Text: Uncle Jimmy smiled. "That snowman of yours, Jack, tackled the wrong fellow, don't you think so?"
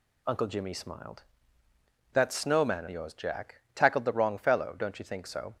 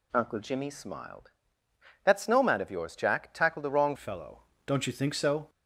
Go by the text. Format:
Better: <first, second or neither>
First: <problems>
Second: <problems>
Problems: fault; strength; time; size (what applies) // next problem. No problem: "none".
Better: first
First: none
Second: changes voice at "fellow"; from 3.9 s on; 1.5 s long